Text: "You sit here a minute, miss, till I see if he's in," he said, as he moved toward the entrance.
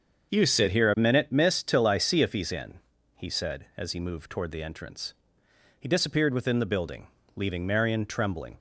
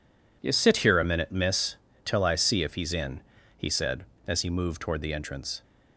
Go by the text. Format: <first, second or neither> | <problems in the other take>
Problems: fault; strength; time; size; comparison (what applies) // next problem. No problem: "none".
second | starts louder than the rest; until 1.3 s; 7 dB // goes on to say "He disappeared within the building leaving Marion trembling"; strong; from 5.7 s on; 2.8 s long